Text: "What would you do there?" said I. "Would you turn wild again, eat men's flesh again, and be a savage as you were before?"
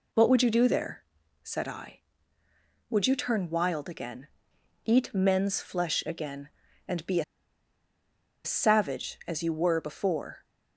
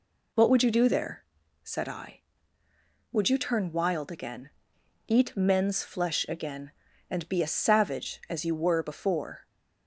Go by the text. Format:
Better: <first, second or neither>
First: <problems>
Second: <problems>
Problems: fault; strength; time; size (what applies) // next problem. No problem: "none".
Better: second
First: pauses between "a" and "savage"; at 7.2 s; 1.2 s long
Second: none